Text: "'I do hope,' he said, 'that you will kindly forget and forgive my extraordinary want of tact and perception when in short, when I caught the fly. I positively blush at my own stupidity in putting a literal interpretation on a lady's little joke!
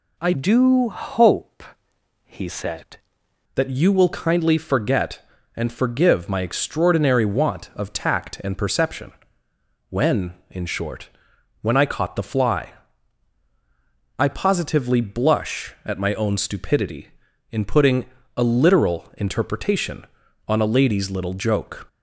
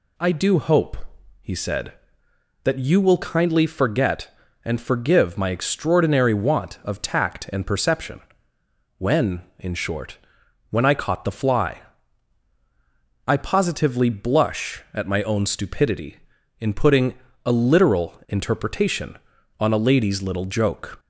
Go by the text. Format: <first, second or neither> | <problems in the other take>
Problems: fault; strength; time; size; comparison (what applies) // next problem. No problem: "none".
second | changes voice from "do" to "said"; from 0.3 to 2.9 s; 2.6 s long // pauses between "perception" and "when"; noticeable; at 9.1 s; 0.78 s long; noticeable in the second // pauses between "putting" and "a"; slight; at 18.0 s; 0.30 s long; slight in the second